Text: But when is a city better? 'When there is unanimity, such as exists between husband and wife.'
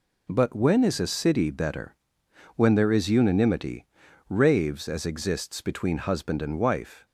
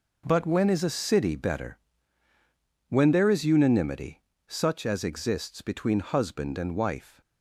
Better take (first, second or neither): second